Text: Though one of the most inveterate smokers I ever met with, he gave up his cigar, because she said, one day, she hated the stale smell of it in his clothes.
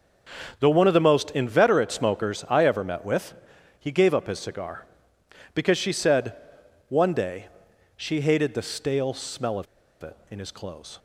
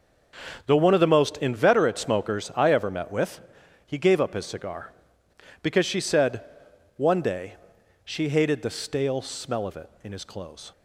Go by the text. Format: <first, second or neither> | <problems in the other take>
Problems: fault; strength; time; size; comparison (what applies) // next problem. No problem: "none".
second | starts louder than the rest; until 1.6 s; 7 dB; also in the second // pauses between "of" and "it"; at 9.6 s; 0.36 s long